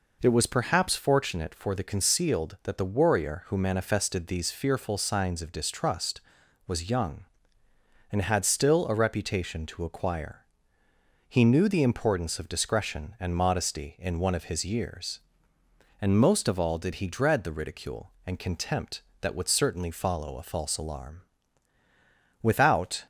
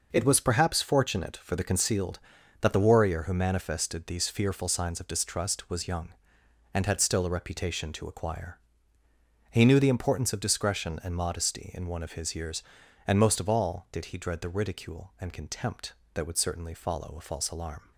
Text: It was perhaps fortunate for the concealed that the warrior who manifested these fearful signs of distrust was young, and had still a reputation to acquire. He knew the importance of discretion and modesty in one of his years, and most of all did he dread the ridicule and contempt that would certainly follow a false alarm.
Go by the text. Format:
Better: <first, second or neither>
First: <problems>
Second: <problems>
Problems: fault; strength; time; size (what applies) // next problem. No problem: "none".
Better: second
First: goes on to say "Without"; noticeable; from 22.4 s on; 0.64 s long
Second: none